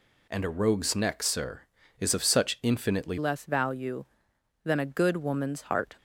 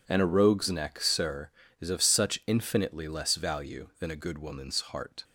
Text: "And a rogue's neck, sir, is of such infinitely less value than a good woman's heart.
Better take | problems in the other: second | changes voice at "less"; from 3.1 s on; 2.8 s long

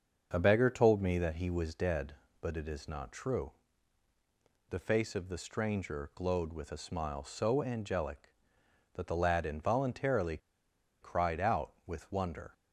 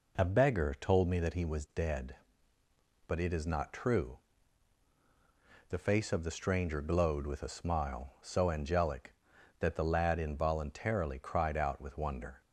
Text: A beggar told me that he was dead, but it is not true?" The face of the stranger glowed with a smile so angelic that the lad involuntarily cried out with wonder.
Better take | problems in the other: second | starts louder than the rest; until 1.3 s; 6.5 dB // pauses between "involuntarily" and "cried"; noticeable; at 10.3 s; 0.63 s long

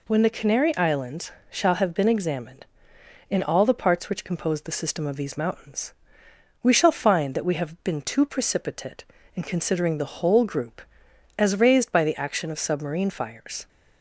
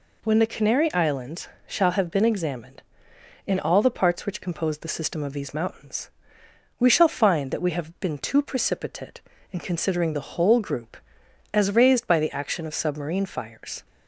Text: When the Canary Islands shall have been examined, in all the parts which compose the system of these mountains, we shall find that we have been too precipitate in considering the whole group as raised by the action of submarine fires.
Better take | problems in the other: neither | pauses between "Islands" and "shall"; slight; the same in both

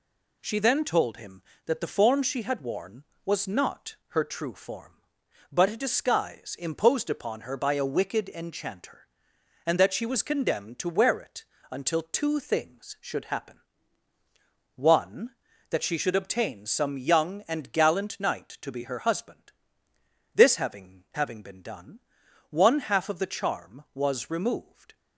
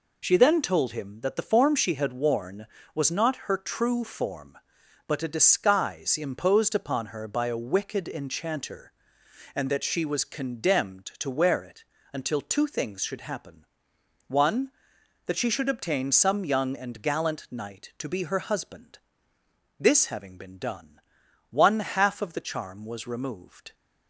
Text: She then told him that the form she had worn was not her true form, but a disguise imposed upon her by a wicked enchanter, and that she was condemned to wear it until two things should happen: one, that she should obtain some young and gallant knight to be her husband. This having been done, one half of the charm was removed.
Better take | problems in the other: second | pauses between "it" and "until"; slight; at 11.4 s; 0.26 s long; slight in the second // says "having" twice; at 21.1 s

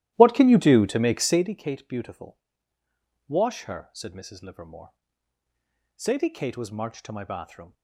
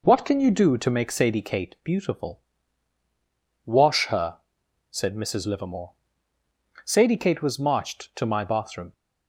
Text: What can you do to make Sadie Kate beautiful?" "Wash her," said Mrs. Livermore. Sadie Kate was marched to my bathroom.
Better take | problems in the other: second | starts louder than the rest; strong; until 1.5 s; 14 dB

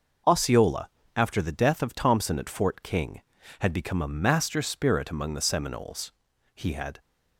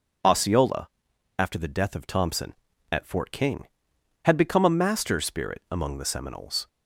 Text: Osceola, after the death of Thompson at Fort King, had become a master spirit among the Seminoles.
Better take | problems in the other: second | goes on to say "He had"; slight; from 6.5 s on; 0.44 s long

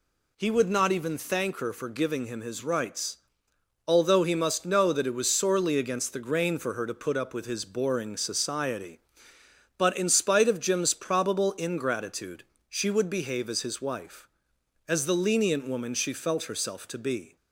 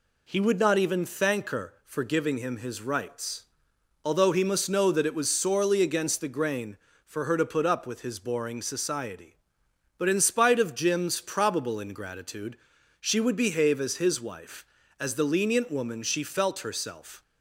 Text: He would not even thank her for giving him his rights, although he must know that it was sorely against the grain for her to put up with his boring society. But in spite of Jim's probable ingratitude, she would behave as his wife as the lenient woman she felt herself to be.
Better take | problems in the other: first | stops before "to be"; at 17.2 s

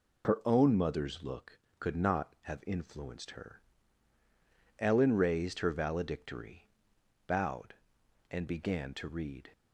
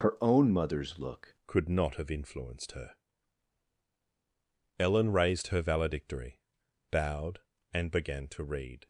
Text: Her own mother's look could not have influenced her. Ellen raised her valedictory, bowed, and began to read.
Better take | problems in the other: first | changes voice at "could"; from 1.4 s on; 7.4 s long

